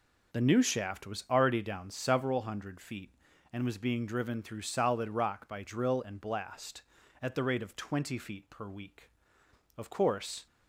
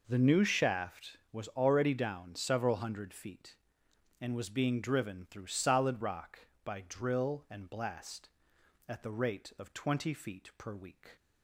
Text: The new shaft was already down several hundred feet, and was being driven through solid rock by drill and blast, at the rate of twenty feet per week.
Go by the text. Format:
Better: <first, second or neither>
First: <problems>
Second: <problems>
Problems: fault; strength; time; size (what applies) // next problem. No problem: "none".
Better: second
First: goes on to say "Of course"; noticeable; from 9.7 s on; 0.70 s long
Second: none